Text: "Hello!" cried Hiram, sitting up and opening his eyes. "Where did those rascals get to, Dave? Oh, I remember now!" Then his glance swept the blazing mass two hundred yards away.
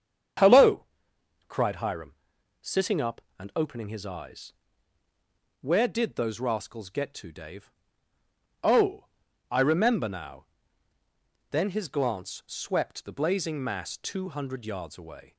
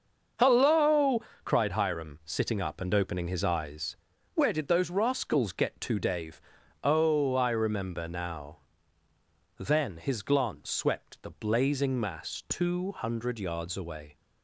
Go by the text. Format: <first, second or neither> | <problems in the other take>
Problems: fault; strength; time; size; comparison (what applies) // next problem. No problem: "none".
neither | starts louder than the rest; the same in both